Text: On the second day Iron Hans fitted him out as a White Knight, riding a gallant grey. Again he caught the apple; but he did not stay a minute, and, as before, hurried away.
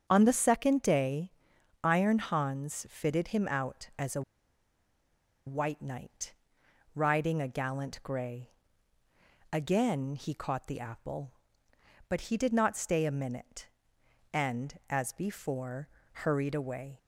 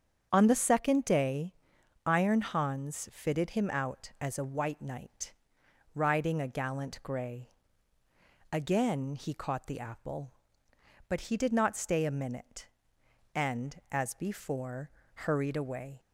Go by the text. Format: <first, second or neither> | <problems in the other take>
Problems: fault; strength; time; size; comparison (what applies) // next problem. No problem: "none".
second | starts louder than the rest; strong; until 1.0 s; 7.5 dB; strong in the second // pauses between "day" and "Iron"; noticeable; at 1.3 s; 0.52 s long; noticeable in the second // pauses between "a" and "White"; strong; at 4.2 s; 1.2 s long